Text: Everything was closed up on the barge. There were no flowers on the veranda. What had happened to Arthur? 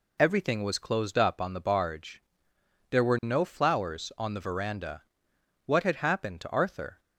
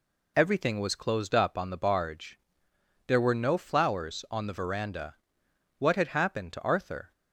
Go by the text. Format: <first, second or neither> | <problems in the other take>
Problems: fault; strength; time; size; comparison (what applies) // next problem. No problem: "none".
neither | none